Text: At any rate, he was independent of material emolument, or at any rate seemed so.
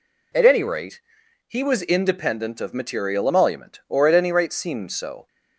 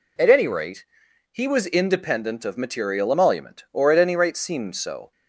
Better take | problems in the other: neither | none

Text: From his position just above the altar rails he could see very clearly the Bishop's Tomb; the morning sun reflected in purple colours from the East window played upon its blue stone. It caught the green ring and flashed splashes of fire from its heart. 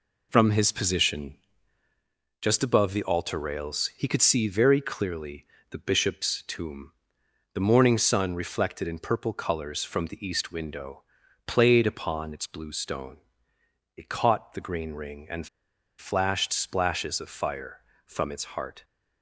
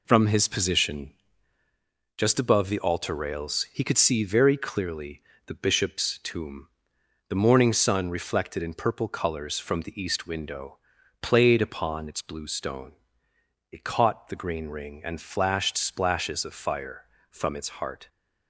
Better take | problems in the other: second | pauses between "position" and "just"; at 1.3 s; 1.0 s long; also in the second // pauses between "clearly" and "the"; slight; at 5.4 s; 0.26 s long; slight in the second // pauses between "window" and "played"; noticeable; at 11.0 s; 0.46 s long; noticeable in the second // pauses between "and" and "flashed"; noticeable; at 15.4 s; 0.50 s long

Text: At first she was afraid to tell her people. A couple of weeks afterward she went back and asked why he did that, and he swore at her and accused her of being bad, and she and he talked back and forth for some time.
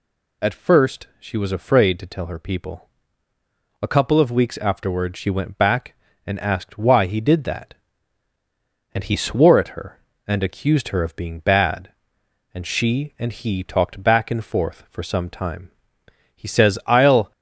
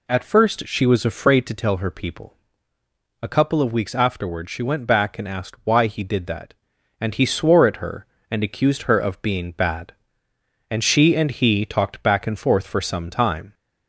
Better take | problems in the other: second | goes on to say "He says I'll"; noticeable; from 16.3 s on; 0.96 s long

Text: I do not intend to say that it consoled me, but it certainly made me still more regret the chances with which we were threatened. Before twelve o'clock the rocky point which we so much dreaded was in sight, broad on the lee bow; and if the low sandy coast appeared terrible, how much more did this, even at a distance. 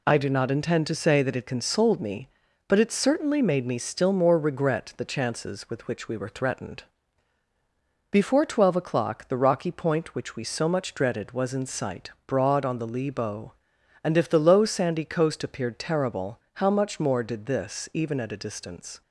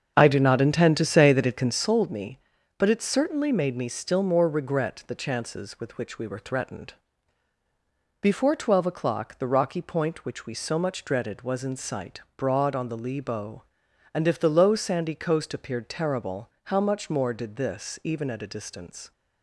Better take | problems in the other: first | starts louder than the rest; until 1.8 s; 7 dB

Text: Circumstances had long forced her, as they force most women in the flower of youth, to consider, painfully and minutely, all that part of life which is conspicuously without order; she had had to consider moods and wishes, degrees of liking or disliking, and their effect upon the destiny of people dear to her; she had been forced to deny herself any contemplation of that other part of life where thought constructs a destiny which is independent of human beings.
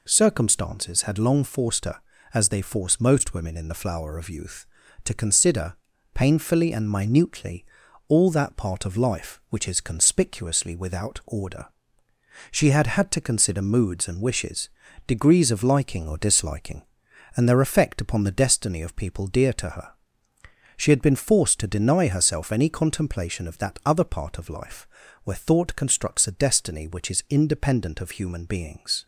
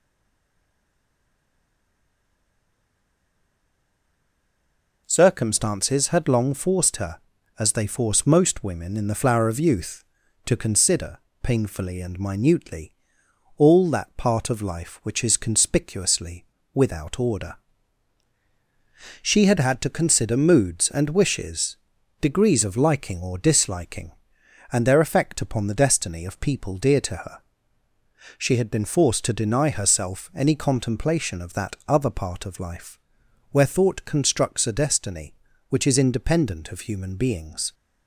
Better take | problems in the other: first | stays silent before the first word; strong; until 5.0 s; 5.0 s long // pauses between "conspicuously" and "without"; slight; at 16.4 s; 0.30 s long // pauses between "life" and "where"; noticeable; at 32.9 s; 0.54 s long; also in the first

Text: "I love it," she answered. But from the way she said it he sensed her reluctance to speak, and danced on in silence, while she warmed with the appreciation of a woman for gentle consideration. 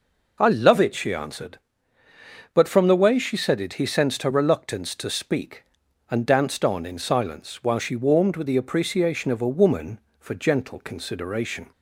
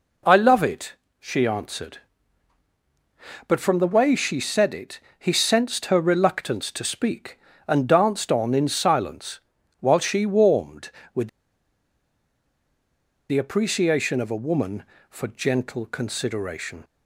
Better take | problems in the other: first | pauses between "it" and "he"; slight; at 4.9 s; 0.20 s long // pauses between "with" and "the"; strong; at 11.2 s; 2.0 s long

